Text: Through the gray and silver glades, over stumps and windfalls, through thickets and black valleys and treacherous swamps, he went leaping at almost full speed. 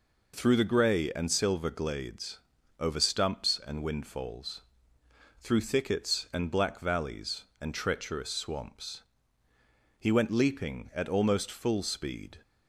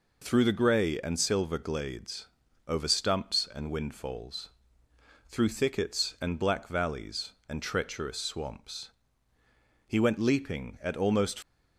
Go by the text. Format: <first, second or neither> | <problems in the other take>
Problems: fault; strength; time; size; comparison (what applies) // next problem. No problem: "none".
first | stops before "full speed"; at 11.4 s